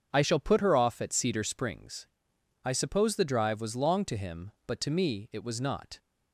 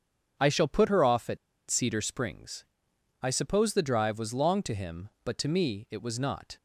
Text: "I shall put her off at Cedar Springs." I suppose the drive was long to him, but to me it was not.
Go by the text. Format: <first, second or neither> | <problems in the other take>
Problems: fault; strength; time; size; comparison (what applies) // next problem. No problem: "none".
first | starts louder than the rest; strong; until 1.7 s; 7.5 dB; strong in the first // pauses between "at" and "Cedar"; slight; at 1.3 s; 0.31 s long